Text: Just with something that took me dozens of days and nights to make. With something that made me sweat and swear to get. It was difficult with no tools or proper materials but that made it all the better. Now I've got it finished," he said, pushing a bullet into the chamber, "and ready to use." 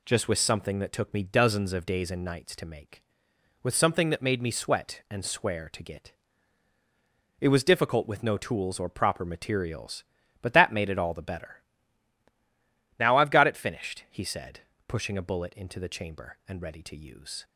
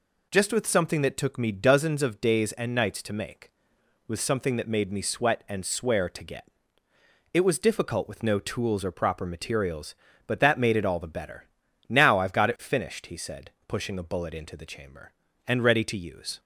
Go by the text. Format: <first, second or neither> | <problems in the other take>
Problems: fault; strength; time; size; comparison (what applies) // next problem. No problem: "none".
neither | none